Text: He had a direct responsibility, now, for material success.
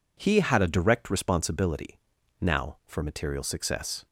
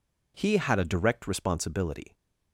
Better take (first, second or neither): first